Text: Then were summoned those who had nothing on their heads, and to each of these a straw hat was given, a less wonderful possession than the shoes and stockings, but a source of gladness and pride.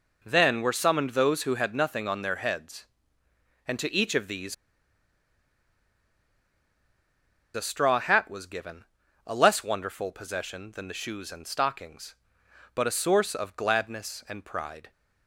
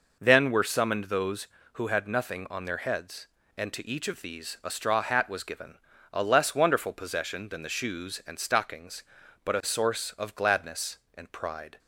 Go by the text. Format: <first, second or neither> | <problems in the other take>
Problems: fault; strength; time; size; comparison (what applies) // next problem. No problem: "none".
second | pauses between "these" and "a"; strong; at 4.5 s; 3.0 s long